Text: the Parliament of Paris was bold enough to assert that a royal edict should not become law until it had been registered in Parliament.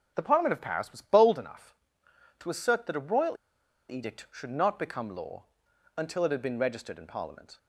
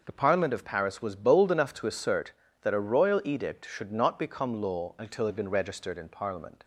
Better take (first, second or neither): second